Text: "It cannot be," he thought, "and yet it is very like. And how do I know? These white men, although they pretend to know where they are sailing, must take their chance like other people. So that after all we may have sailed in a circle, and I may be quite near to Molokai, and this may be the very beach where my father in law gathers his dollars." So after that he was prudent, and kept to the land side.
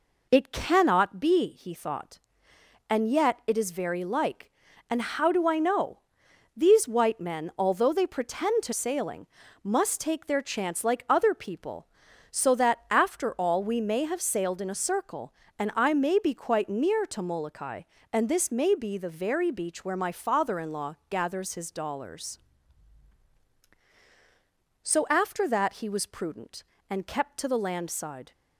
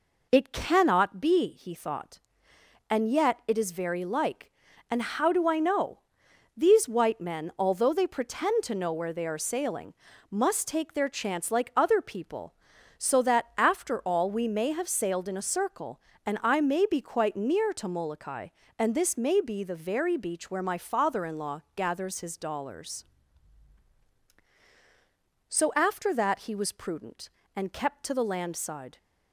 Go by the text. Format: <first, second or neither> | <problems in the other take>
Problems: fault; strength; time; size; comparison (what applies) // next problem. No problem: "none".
second | skips "know where they are"; at 8.7 s